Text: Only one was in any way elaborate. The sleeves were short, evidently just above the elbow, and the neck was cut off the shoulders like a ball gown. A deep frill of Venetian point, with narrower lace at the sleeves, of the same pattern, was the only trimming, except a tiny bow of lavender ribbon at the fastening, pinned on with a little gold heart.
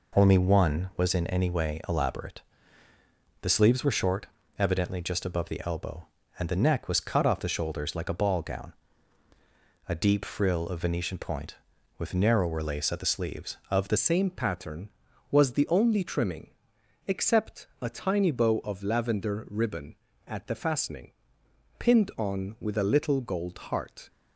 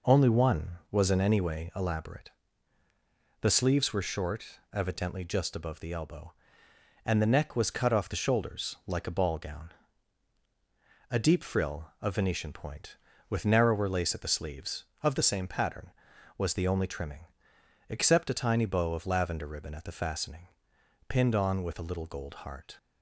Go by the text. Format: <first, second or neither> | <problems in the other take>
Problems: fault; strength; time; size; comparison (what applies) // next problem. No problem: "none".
second | changes voice at "same"; from 13.9 s on; 10.1 s long